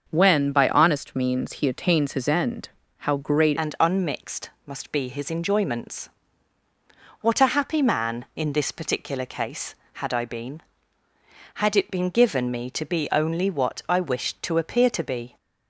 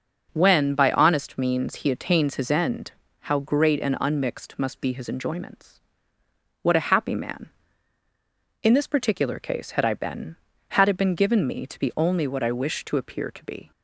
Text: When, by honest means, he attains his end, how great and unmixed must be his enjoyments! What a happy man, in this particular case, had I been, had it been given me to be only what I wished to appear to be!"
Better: second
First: starts louder than the rest; until 1.1 s; 6.5 dB // changes voice at "and"; from 3.5 s on; 11.8 s long // pauses between "unmixed" and "must"; slight; at 4.5 s; 0.16 s long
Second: none

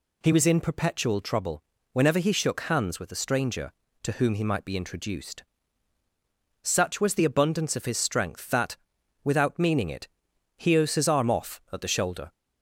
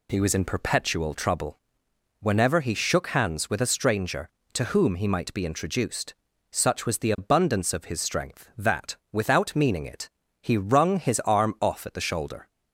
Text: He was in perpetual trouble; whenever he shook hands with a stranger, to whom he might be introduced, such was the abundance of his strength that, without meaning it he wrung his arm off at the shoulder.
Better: second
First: pauses between "it" and "he"; noticeable; at 10.0 s; 0.50 s long // skips "wrung"; at 10.7 s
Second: pauses between "it" and "he"; slight; at 10.0 s; 0.30 s long

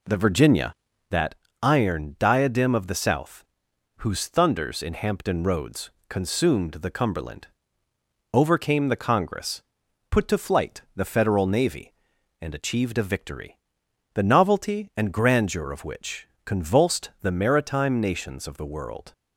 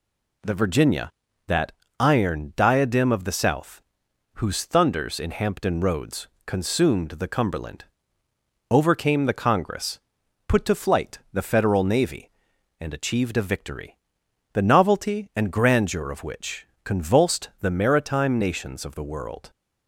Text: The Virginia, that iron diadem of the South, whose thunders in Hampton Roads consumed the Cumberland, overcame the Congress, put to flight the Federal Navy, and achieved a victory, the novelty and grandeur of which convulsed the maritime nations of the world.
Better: second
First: starts louder than the rest; slight; until 1.1 s; 2.5 dB // pauses between "that" and "iron"; slight; at 1.3 s; 0.26 s long // pauses between "Roads" and "consumed"; slight; at 5.9 s; 0.18 s long // pauses between "which" and "convulsed"; slight; at 16.2 s; 0.20 s long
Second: pauses between "that" and "iron"; slight; at 1.7 s; 0.26 s long // pauses between "Roads" and "consumed"; slight; at 6.2 s; 0.18 s long // pauses between "which" and "convulsed"; slight; at 16.6 s; 0.20 s long

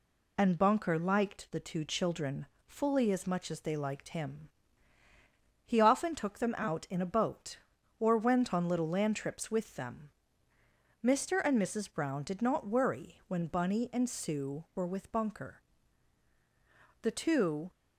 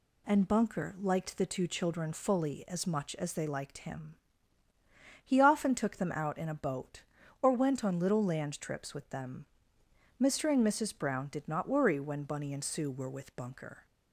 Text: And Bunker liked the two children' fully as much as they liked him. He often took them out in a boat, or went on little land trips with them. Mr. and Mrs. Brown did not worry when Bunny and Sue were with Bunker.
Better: second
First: pauses between "children" and "fully"; slight; at 2.4 s; 0.20 s long // goes on to say "The two"; noticeable; from 17.0 s on; 0.68 s long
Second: none

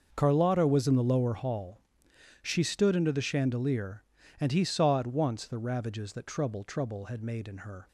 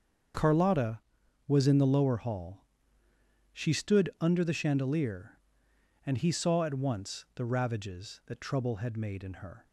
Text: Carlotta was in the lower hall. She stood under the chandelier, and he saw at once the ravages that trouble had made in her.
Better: second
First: starts louder than the rest; until 1.1 s; 6 dB // says "trouble" twice; at 6.6 s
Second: starts louder than the rest; until 1.8 s; 7 dB

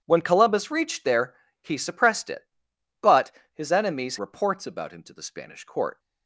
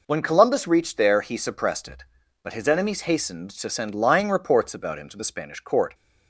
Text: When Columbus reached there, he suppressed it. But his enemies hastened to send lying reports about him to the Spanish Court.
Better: second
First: pauses between "But" and "his"; slight; at 3.3 s; 0.22 s long // skips "hastened to send lying"; at 4.1 s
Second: none

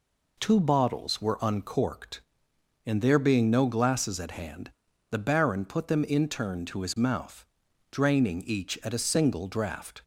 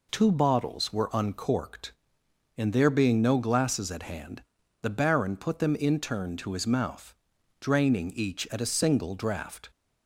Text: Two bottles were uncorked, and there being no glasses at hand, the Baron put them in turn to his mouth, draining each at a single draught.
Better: neither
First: none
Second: none

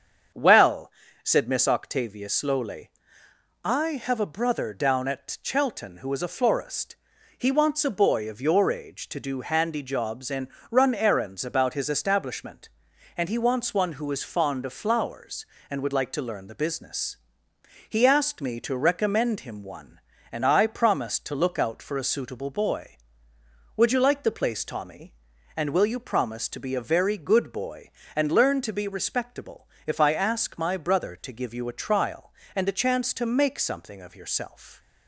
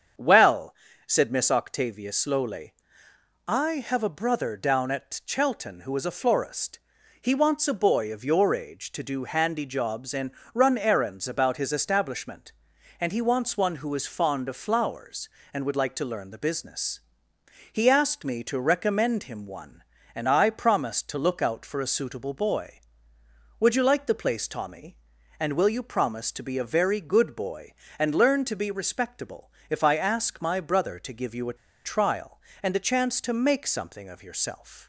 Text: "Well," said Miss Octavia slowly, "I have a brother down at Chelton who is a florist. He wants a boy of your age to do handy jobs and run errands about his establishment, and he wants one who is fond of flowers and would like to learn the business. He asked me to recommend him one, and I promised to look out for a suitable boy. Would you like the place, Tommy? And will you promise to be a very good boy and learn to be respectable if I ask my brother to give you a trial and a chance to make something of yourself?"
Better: first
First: starts louder than the rest; strong; until 1.6 s; 7.5 dB // pauses between "and" and "run"; slight; at 10.4 s; 0.24 s long // pauses between "respectable" and "if"; slight; at 29.6 s; 0.20 s long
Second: starts louder than the rest; strong; until 1.5 s; 7.5 dB // pauses between "and" and "run"; slight; at 10.2 s; 0.24 s long // pauses between "respectable" and "if"; slight; at 29.4 s; 0.20 s long // pauses between "a" and "trial"; slight; at 31.5 s; 0.28 s long

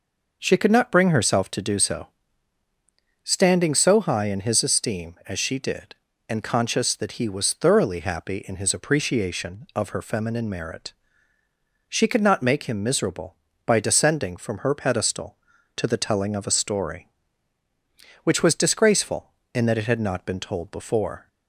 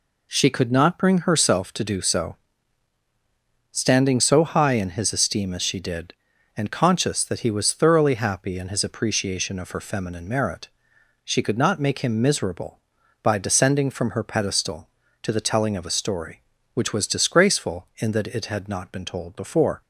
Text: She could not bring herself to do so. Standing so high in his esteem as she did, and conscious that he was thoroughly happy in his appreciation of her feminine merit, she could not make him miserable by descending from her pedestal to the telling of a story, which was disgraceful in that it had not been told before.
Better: neither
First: none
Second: none

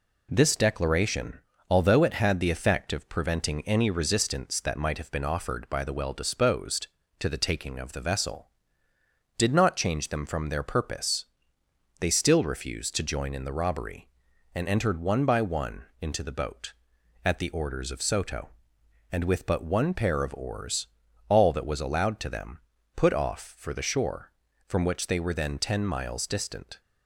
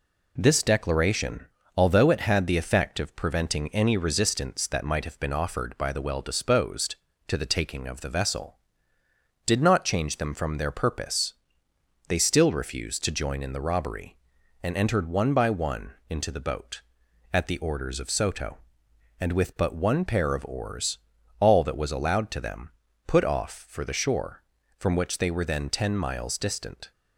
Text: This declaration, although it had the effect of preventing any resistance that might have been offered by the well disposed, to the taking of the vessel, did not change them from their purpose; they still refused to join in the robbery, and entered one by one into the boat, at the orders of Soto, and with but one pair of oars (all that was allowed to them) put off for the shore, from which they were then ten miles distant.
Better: neither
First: pauses between "one" and "into"; slight; at 15.8 s; 0.18 s long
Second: pauses between "one" and "into"; slight; at 15.9 s; 0.18 s long

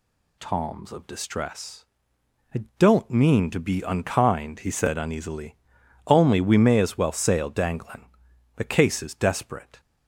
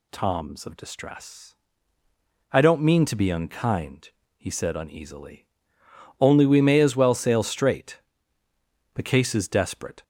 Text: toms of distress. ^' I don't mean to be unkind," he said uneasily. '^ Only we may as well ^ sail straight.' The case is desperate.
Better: second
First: pauses between "I" and "don't"; slight; at 2.6 s; 0.16 s long // says "danglin" for "straight"; at 7.5 s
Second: none

